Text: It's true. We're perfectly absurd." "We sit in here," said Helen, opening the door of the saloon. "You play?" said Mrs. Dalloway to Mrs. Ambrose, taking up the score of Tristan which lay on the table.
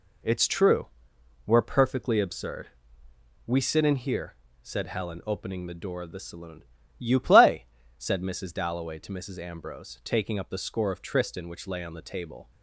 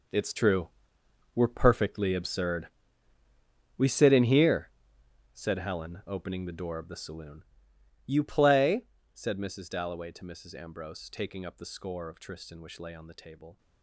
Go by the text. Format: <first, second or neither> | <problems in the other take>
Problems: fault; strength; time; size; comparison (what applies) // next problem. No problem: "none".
first | gets quieter; strong; throughout; 13.5 dB